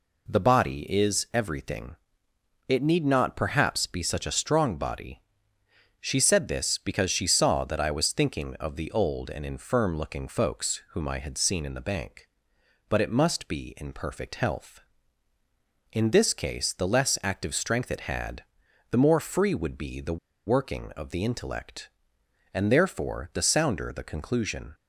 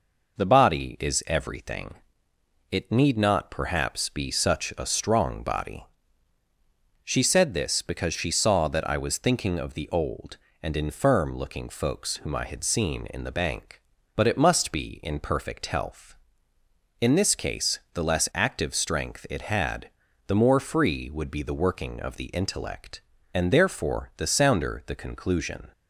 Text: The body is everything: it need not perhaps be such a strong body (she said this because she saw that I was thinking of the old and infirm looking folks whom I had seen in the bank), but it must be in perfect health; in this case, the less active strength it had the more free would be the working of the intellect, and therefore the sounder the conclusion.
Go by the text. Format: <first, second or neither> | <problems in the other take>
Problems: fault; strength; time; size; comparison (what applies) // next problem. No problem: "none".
second | pauses between "had" and "the"; noticeable; at 18.4 s; 0.48 s long; also in the second // pauses between "the" and "working"; slight; at 20.1 s; 0.27 s long